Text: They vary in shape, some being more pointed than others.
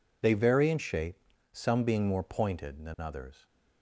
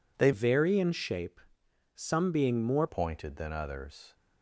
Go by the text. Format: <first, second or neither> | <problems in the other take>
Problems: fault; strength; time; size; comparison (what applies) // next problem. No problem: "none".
first | changes voice from "vary" to "more"; from 0.3 to 2.8 s; 2.5 s long